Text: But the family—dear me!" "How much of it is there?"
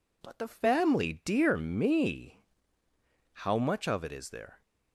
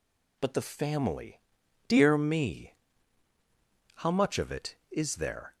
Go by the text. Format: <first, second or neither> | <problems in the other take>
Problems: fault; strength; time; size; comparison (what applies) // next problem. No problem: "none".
neither | none